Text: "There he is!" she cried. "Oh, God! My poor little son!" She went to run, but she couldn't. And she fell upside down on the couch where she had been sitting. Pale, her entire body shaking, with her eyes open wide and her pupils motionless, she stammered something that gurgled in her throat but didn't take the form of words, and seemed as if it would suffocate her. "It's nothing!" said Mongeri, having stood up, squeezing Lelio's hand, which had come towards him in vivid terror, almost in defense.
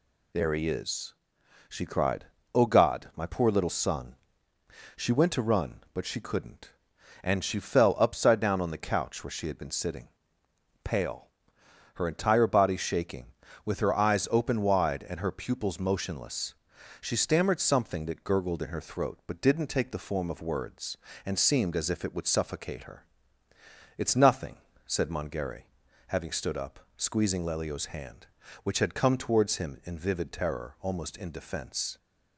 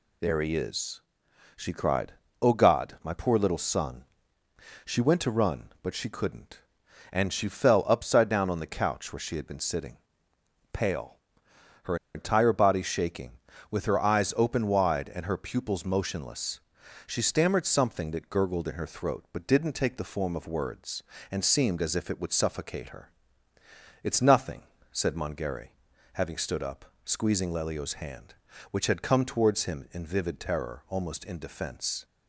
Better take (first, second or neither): first